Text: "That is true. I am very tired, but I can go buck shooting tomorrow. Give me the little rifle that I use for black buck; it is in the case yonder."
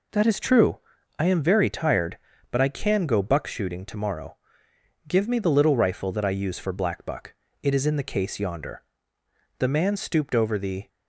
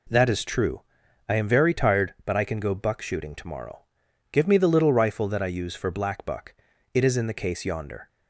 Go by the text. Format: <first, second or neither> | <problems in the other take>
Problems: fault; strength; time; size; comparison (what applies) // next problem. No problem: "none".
second | goes on to say "The man stooped over the"; noticeable; from 9.5 s on; 1.3 s long